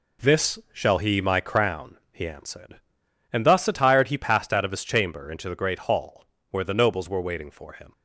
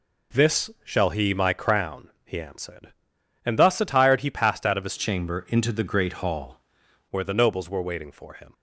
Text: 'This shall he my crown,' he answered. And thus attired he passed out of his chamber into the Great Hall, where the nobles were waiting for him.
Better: first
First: pauses between "This" and "shall"; slight; at 0.5 s; 0.16 s long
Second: pauses between "This" and "shall"; slight; at 0.6 s; 0.16 s long // changes voice from "chamber" to "Hall"; from 4.9 to 6.6 s; 1.7 s long

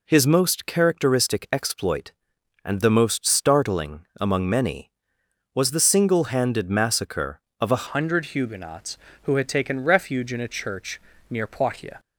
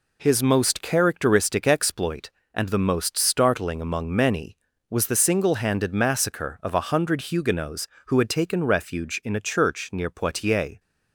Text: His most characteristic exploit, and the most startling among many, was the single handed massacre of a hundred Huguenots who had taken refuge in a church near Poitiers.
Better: second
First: changes voice at "hundred"; from 7.8 s on; 4.1 s long // pauses between "church" and "near"; slight; at 10.9 s; 0.28 s long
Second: none

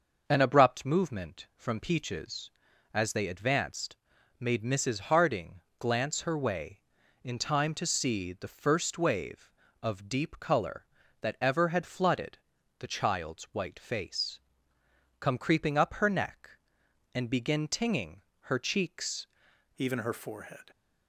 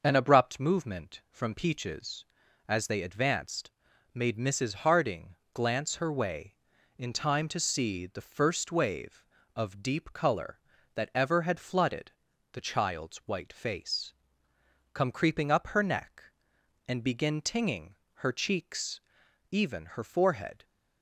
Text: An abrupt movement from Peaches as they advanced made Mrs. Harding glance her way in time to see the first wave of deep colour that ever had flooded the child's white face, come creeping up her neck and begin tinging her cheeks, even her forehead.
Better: second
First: starts louder than the rest; until 1.2 s; 6 dB // pauses between "advanced" and "made"; noticeable; at 3.9 s; 0.46 s long // pauses between "Harding" and "glance"; slight; at 5.5 s; 0.18 s long // pauses between "flooded" and "the"; at 12.3 s; 0.42 s long // pauses between "tinging" and "her"; slight; at 18.2 s; 0.28 s long // changes voice at "even"; from 19.7 s on; 1.0 s long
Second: starts louder than the rest; until 1.0 s; 6 dB // pauses between "advanced" and "made"; noticeable; at 3.6 s; 0.46 s long // pauses between "Harding" and "glance"; slight; at 5.3 s; 0.18 s long // pauses between "flooded" and "the"; at 12.1 s; 0.42 s long // pauses between "tinging" and "her"; slight; at 17.9 s; 0.28 s long

